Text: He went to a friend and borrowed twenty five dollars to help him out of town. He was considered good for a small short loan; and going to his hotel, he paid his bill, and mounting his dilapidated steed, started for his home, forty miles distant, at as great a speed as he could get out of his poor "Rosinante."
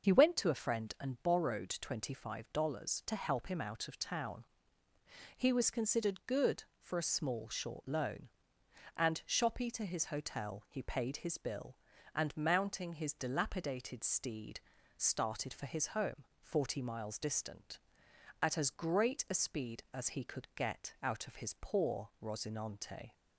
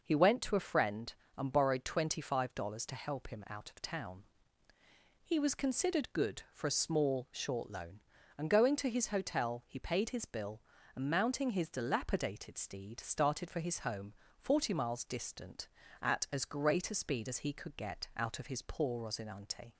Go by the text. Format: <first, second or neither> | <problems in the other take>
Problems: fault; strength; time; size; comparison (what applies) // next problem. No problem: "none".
second | starts louder than the rest; noticeable; until 1.1 s; 6 dB // says "shoppy" for "going"; at 9.2 s